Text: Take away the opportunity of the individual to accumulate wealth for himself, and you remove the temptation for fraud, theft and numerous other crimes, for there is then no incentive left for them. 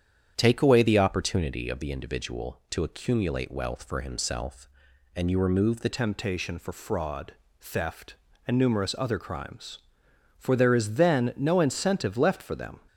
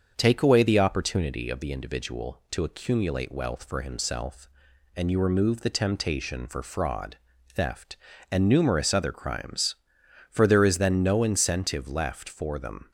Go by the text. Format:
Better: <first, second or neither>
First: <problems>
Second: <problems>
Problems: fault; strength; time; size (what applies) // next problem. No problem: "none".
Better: second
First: starts louder than the rest; strong; until 1.3 s; 8.5 dB // changes voice at "temptation"; from 5.9 s on; 6.8 s long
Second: starts louder than the rest; until 1.1 s; 7 dB